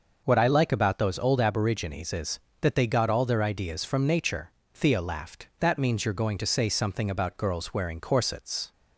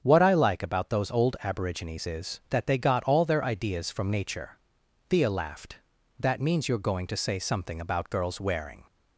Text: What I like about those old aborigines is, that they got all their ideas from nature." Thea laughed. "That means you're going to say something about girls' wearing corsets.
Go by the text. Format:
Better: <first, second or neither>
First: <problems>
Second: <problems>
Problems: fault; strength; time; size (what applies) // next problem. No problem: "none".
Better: first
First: starts louder than the rest; noticeable; until 1.2 s; 6 dB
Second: starts louder than the rest; strong; until 1.0 s; 8 dB // stops before "corsets"; at 8.8 s